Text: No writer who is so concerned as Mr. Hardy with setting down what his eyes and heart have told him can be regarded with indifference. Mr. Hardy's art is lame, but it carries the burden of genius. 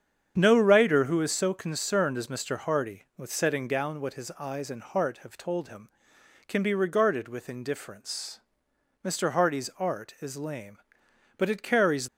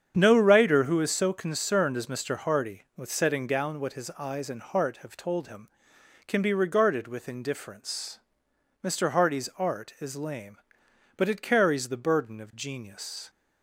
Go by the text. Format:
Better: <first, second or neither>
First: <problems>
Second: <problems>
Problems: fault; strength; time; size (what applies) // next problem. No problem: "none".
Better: second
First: starts louder than the rest; strong; until 1.3 s; 8 dB // stops before "the burden of genius"; at 12.0 s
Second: starts louder than the rest; strong; until 1.1 s; 8 dB